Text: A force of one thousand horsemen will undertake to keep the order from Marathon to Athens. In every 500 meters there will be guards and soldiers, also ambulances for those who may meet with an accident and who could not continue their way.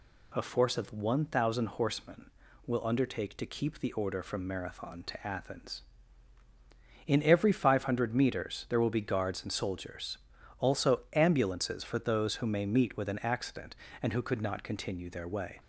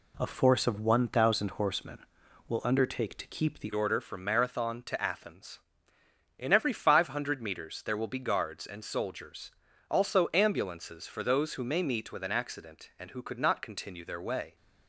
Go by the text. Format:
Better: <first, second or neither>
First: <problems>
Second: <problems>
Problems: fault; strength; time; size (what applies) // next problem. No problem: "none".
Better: first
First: none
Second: changes voice at "order"; from 3.7 s on; 10.8 s long